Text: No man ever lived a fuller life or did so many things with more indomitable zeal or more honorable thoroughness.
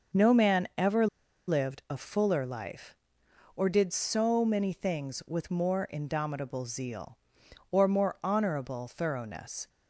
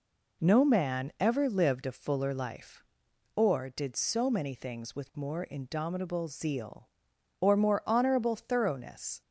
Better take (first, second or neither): second